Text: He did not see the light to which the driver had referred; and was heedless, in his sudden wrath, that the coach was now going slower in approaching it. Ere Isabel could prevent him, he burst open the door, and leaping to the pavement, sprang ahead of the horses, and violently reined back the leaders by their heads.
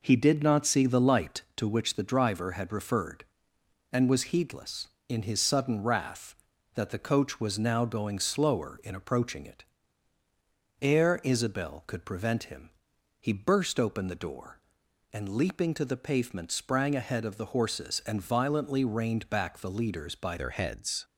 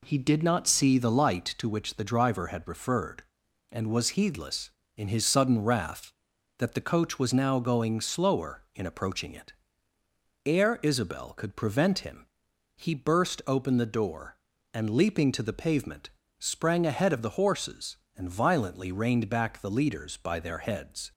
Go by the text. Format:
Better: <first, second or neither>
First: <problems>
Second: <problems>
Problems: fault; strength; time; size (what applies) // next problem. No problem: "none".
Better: second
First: changes voice at "their"; from 20.3 s on; 0.7 s long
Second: none